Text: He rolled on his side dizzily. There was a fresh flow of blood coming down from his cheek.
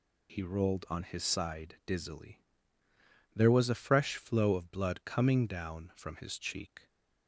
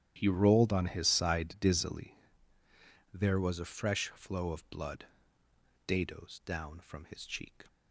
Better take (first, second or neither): first